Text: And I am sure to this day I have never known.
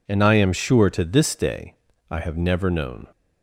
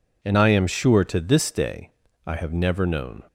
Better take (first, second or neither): neither